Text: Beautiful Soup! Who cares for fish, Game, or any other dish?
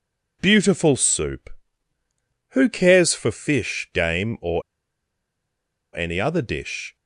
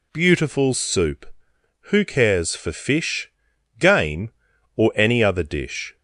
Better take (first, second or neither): second